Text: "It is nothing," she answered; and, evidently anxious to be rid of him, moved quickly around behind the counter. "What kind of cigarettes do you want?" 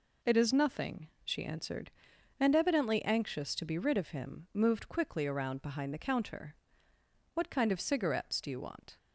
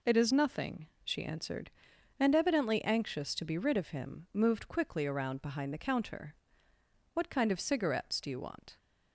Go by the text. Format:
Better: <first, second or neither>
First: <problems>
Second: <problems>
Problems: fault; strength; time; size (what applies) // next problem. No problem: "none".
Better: neither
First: none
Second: none